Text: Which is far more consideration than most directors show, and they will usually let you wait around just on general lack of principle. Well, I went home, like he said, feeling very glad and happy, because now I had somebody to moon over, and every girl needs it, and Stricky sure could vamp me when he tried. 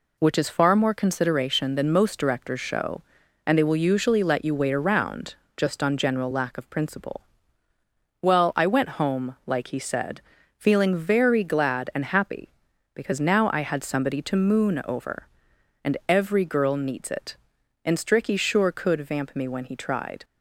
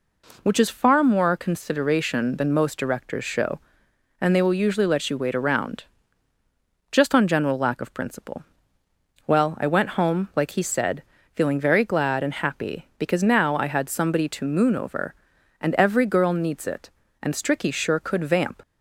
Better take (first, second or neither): first